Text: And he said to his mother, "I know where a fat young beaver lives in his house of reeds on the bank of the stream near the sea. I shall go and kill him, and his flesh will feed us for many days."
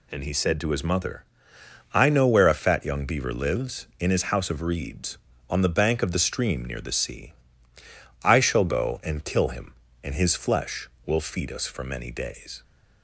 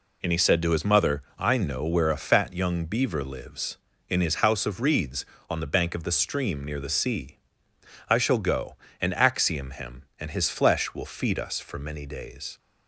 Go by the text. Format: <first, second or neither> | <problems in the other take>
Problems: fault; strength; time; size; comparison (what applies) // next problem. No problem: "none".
first | says "axiom" for "kill"; at 9.1 s